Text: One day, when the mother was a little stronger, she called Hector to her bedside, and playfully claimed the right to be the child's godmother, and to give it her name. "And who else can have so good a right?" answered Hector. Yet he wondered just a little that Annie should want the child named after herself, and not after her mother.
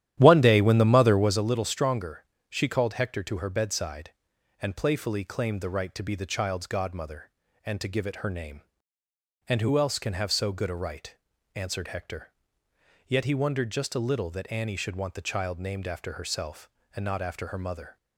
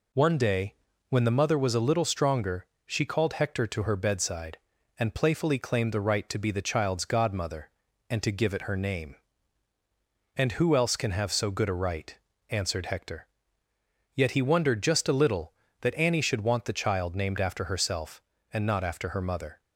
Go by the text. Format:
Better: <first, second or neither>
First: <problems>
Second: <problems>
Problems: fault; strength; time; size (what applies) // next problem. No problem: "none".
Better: second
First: starts louder than the rest; strong; until 1.5 s; 12 dB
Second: none